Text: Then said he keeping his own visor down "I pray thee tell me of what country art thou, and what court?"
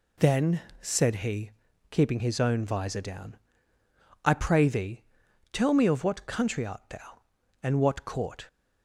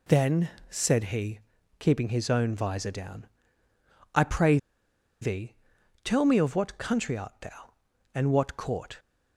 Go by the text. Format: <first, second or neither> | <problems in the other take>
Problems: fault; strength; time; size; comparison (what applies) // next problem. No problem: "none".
first | pauses between "Then" and "said"; slight; at 0.4 s; 0.20 s long; slight in the first // pauses between "he" and "keeping"; at 1.3 s; 0.40 s long; also in the first // pauses between "down" and "I"; noticeable; at 3.2 s; 0.90 s long; noticeable in the first // pauses between "pray" and "thee"; noticeable; at 4.5 s; 0.64 s long // pauses between "thee" and "tell"; noticeable; at 5.5 s; 0.48 s long; noticeable in the first